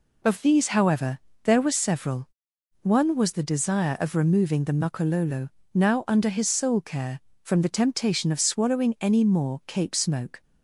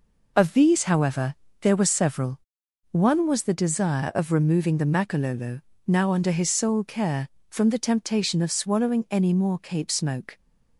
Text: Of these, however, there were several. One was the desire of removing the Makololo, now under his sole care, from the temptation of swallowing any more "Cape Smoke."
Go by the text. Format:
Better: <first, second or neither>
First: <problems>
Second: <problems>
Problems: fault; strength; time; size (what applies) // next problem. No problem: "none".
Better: neither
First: none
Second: none